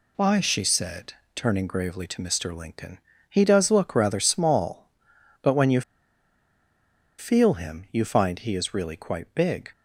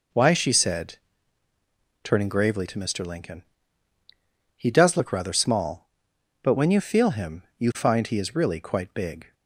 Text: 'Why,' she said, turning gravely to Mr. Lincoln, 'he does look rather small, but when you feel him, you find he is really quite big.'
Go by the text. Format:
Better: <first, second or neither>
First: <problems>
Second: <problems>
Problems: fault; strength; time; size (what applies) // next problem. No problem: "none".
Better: second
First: pauses between "you" and "feel"; strong; at 5.8 s; 1.3 s long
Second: none